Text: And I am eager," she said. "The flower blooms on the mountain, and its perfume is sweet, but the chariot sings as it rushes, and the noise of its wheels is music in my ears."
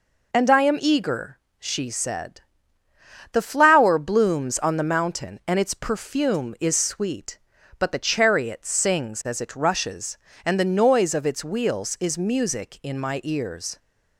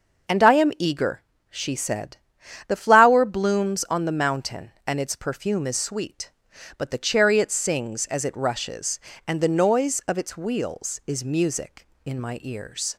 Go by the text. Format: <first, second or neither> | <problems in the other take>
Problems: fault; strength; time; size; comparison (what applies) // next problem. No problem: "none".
neither | none